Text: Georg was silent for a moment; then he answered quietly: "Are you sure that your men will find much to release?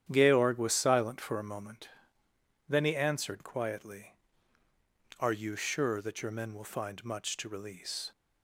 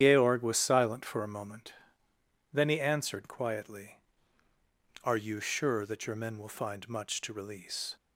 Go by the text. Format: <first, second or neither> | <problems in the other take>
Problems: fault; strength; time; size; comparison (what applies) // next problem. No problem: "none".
first | loses the start of "Georg"; at 0.0 s; 80 ms // starts louder than the rest; strong; until 1.0 s; 9.5 dB; strong in the first